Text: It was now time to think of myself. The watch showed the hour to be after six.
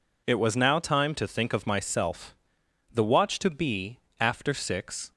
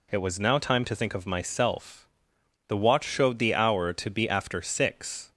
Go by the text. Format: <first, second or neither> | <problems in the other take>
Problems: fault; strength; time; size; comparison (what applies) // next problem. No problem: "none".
second | skips "showed the hour"; at 3.3 s // pauses between "be" and "after"; slight; at 3.9 s; 0.20 s long